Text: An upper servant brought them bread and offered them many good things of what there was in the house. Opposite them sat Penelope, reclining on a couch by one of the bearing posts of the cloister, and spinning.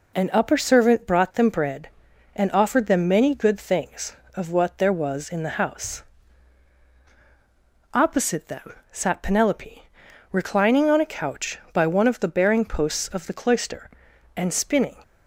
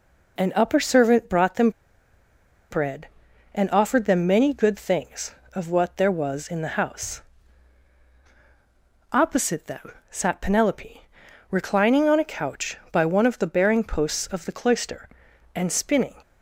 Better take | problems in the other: first | pauses between "them" and "bread"; at 1.6 s; 1.0 s long // pauses between "them" and "sat"; slight; at 9.9 s; 0.18 s long; slight in the first

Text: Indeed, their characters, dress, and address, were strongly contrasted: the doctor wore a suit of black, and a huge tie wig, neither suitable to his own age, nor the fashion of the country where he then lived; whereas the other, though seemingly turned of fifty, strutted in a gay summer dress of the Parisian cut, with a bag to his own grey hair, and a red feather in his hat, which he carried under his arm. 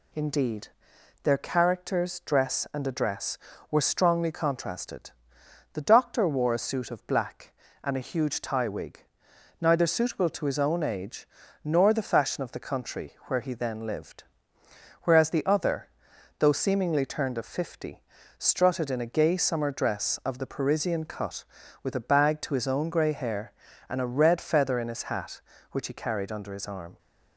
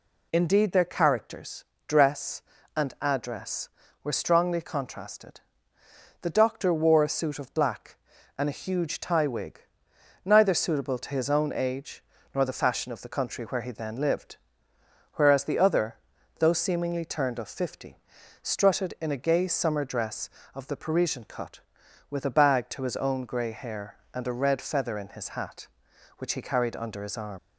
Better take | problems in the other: first | leaves "arm" unfinished; at 27.3 s; 75 ms

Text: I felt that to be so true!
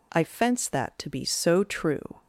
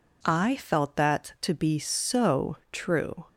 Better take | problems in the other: second | says "fence" for "felt"; at 0.2 s

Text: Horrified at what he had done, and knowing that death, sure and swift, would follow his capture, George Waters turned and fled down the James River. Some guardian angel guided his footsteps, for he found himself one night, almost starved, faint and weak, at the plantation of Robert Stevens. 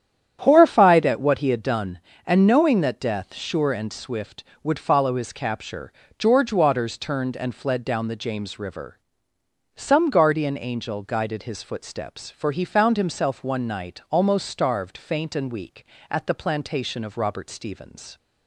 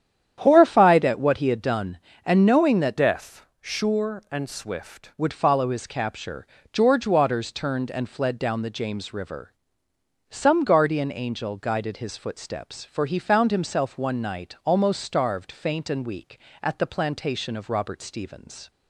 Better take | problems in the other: first | starts louder than the rest; strong; until 1.3 s; 9.5 dB; strong in the first // changes voice from "death" to "swift"; from 2.9 to 5.1 s; 2.2 s long

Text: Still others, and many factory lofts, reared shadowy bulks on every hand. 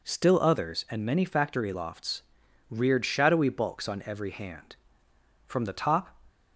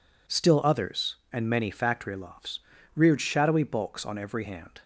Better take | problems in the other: second | goes on to say "From the top"; noticeable; from 5.4 s on; 0.70 s long

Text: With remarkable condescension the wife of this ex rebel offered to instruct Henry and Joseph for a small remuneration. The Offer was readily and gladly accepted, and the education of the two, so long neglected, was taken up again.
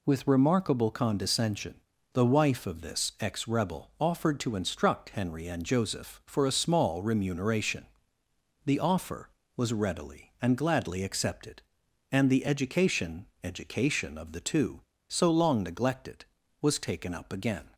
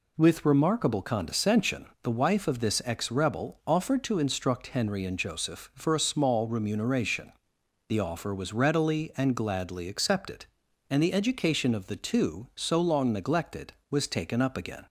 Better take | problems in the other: second | pauses between "condescension" and "the"; slight; at 1.7 s; 0.36 s long; slight in the second // says "education" twice; at 13.4 s

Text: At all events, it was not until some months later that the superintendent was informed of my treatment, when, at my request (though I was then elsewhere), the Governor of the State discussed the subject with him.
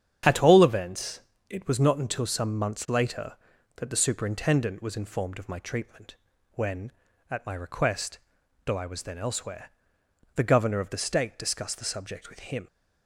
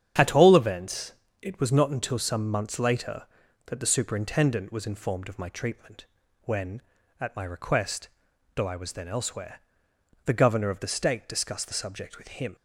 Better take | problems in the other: neither | starts louder than the rest; strong; the same in both

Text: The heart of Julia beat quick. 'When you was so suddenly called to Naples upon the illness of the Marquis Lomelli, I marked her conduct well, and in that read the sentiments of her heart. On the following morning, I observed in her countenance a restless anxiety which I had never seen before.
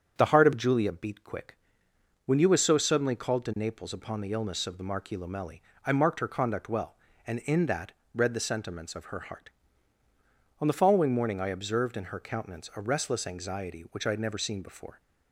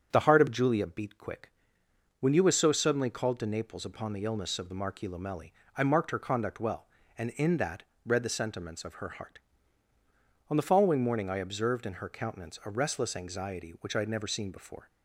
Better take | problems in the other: neither | starts louder than the rest; strong; the same in both // pauses between "that" and "read"; slight; the same in both

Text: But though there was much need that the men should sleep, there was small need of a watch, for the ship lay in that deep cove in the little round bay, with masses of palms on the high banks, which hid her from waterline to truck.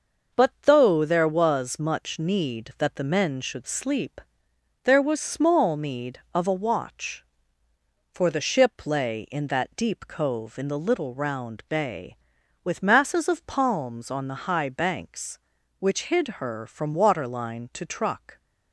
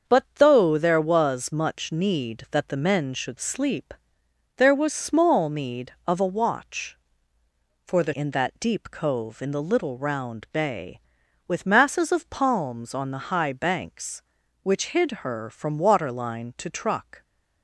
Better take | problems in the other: first | starts louder than the rest; until 1.1 s; 7 dB; noticeable in the first // skips "ship lay"; at 8.1 s

